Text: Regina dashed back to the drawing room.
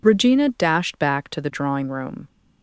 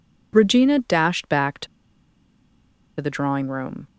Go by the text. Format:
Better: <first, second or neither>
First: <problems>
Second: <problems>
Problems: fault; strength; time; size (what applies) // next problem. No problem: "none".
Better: first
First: none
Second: pauses between "to" and "the"; strong; at 1.6 s; 1.3 s long